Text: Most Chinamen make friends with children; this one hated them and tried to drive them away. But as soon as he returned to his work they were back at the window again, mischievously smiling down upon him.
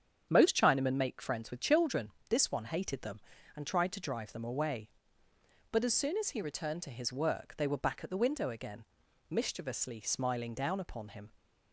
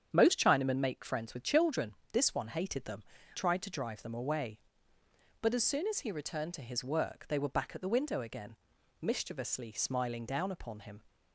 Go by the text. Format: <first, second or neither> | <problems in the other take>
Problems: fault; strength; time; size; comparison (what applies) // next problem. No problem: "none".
first | starts louder than the rest; strong; until 1.1 s; 8 dB; strong in the first // skips "and"; at 3.1 s